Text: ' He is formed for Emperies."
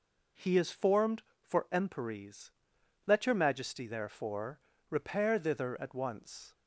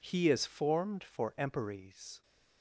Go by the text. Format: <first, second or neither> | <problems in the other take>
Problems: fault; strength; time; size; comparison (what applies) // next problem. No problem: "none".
second | goes on to say "Let your Majesty therefore repair thither at once"; strong; from 3.0 s on; 3.4 s long